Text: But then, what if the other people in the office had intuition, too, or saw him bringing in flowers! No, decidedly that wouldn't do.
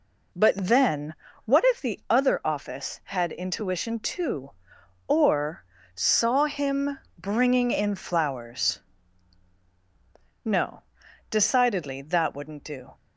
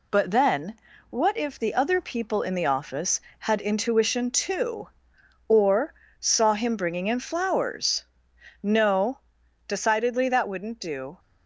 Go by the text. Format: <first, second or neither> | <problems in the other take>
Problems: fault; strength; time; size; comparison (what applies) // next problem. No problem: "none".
second | skips "people in the"; at 2.4 s // pauses between "or" and "saw"; slight; at 5.6 s; 0.32 s long; slight in the second // pauses between "him" and "bringing"; slight; at 6.9 s; 0.20 s long